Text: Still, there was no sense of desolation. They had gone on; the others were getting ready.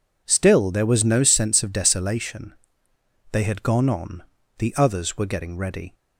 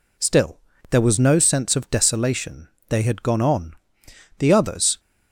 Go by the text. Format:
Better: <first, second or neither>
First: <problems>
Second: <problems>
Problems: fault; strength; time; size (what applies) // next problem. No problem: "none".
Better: first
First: none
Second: stops before "were getting ready"; at 4.9 s